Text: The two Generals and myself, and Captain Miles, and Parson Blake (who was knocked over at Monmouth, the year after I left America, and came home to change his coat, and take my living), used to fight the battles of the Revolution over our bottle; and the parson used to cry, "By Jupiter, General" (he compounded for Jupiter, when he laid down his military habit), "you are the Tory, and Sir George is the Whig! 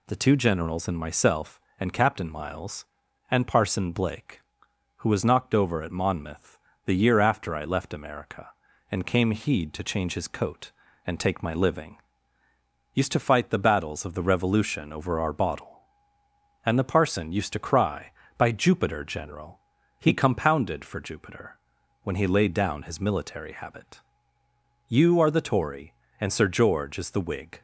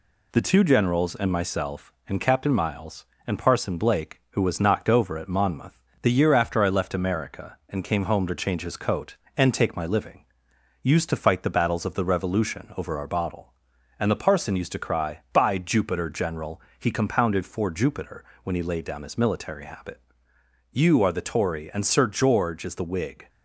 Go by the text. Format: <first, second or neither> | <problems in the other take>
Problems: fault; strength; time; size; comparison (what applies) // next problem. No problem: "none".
second | says "heed" for "home"; at 9.3 s